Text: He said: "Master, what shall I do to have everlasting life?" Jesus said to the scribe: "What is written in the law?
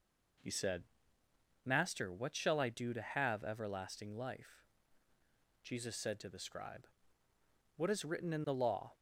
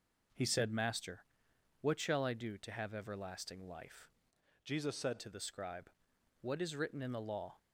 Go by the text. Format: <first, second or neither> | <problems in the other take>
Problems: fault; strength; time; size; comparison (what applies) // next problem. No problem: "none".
first | changes voice from "Jesus" to "said"; from 4.6 to 5.1 s; 0.5 s long